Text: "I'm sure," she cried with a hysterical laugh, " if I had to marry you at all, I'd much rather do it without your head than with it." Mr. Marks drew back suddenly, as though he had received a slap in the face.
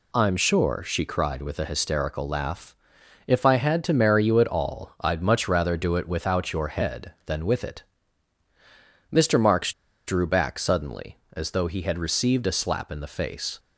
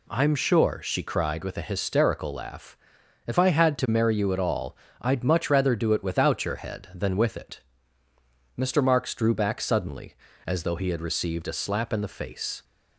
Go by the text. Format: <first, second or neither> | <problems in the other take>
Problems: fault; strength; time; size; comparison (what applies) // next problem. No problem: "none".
second | pauses between "Marks" and "drew"; slight; at 9.7 s; 0.35 s long